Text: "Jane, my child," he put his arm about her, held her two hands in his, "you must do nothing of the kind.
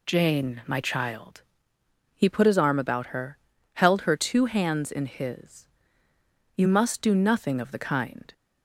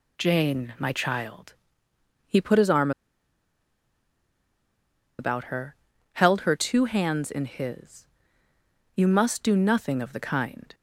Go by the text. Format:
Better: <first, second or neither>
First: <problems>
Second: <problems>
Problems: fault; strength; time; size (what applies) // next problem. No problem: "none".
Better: first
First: none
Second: pauses between "arm" and "about"; strong; at 2.9 s; 2.2 s long